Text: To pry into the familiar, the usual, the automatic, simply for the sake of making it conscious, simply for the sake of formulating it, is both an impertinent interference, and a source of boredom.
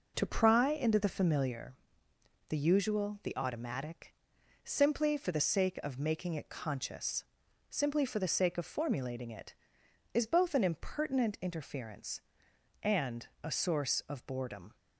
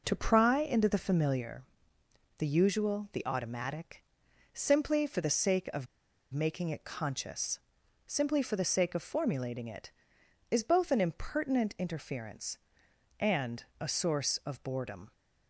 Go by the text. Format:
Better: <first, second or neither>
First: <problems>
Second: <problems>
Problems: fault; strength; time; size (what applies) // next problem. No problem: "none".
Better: first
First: pauses between "and" and "a"; slight; at 13.2 s; 0.18 s long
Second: pauses between "of" and "making"; noticeable; at 5.8 s; 0.47 s long // pauses between "and" and "a"; slight; at 13.6 s; 0.18 s long